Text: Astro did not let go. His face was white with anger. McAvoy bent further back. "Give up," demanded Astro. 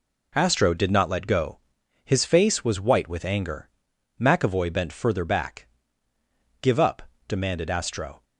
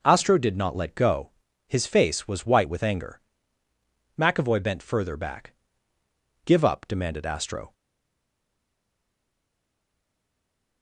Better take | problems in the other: first | stays silent after the last word; strong; from 7.7 s on; 3.1 s long

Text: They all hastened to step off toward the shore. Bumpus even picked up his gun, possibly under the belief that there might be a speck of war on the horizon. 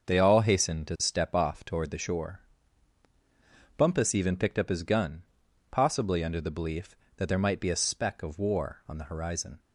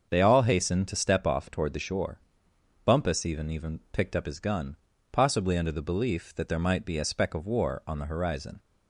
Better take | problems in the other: first | starts louder than the rest; until 1.1 s; 6.5 dB; also in the first // says "even" twice; at 3.4 s

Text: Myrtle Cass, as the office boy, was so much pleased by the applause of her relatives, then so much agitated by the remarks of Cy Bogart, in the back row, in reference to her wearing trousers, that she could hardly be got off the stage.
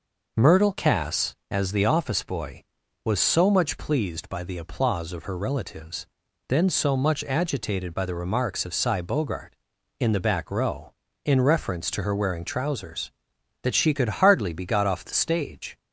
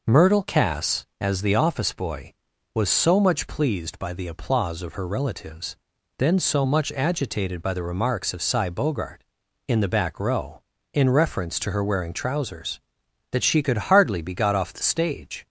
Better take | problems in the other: neither | none

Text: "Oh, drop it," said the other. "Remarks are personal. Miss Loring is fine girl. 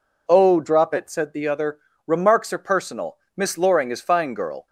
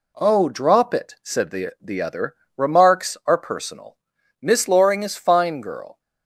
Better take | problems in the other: first | says "the" twice; at 1.8 s

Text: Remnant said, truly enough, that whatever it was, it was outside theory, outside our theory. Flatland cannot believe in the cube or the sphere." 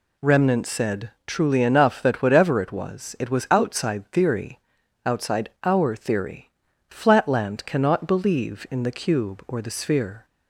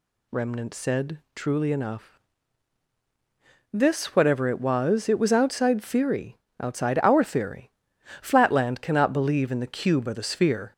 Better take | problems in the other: first | says "this" for "that"; at 3.7 s

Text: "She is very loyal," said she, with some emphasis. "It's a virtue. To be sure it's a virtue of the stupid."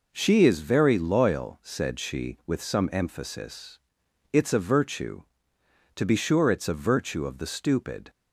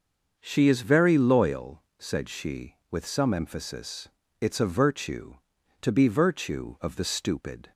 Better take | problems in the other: first | starts louder than the rest; until 1.4 s; 6.5 dB // skips "sure it's a"; at 6.0 s

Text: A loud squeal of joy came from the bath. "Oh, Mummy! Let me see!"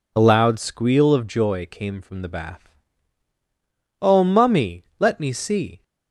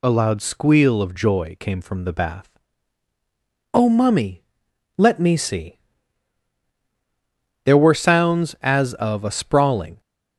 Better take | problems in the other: first | goes on to say "There were sounds as of a sprawling"; strong; from 7.6 s on; 2.3 s long

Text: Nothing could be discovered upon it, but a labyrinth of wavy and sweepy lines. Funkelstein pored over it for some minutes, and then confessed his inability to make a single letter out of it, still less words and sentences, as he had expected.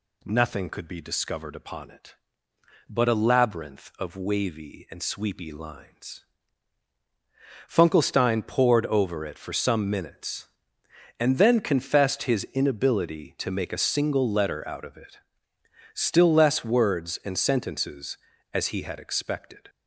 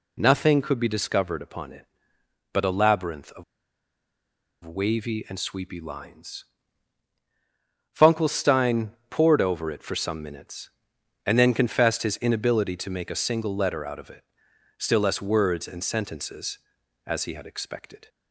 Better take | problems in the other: first | pauses between "of" and "wavy"; at 3.4 s; 1.2 s long // pauses between "Funkelstein" and "pored"; slight; at 8.9 s; 0.18 s long

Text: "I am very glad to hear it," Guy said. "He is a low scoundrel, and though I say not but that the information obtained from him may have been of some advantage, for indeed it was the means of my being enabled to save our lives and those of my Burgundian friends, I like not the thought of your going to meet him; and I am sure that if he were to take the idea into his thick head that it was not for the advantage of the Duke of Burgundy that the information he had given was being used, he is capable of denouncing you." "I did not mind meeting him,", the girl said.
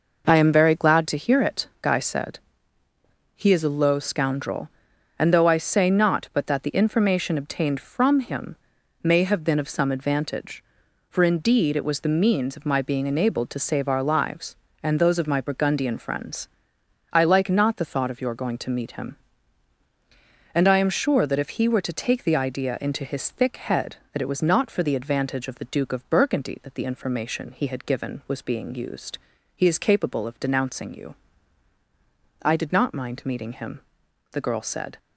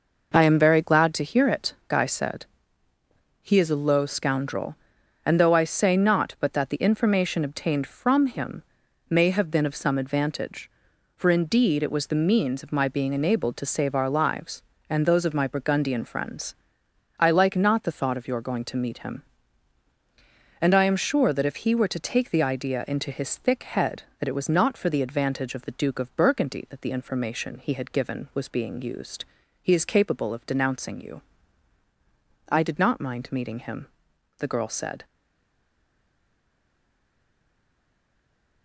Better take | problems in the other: first | pauses between "him" and "may"; noticeable; at 8.6 s; 0.48 s long; noticeable in the first // stays silent after the last word; strong; from 35.0 s on; 3.6 s long

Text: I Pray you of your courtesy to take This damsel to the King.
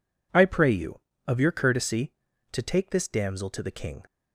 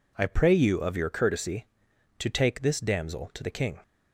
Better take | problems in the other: neither | none

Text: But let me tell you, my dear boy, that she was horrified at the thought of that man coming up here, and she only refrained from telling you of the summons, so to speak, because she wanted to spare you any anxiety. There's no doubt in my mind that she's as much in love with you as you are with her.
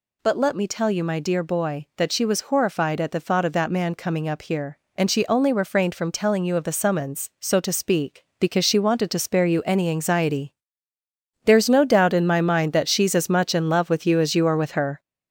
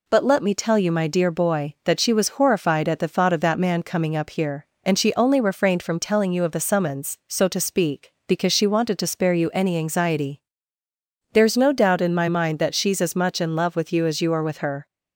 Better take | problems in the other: second | gets louder; noticeable; throughout; 5 dB

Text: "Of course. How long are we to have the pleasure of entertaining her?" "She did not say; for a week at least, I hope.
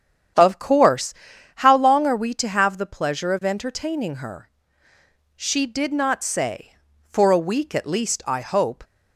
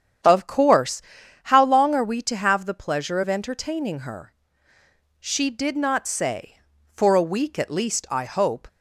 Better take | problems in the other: neither | starts louder than the rest; strong; the same in both

